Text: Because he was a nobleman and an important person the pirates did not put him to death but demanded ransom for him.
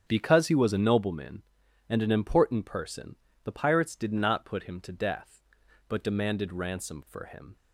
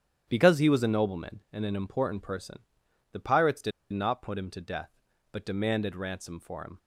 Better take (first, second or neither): first